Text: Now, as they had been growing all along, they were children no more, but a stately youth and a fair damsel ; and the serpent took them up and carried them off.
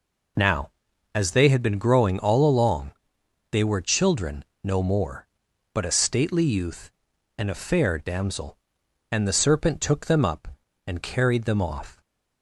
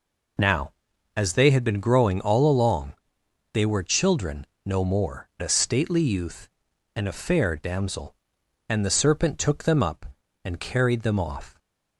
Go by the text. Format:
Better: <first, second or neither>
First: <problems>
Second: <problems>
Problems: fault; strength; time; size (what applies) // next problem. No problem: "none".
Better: first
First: pauses between "children" and "no"; slight; at 4.4 s; 0.20 s long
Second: pauses between "children" and "no"; slight; at 4.4 s; 0.20 s long // skips "but"; at 5.3 s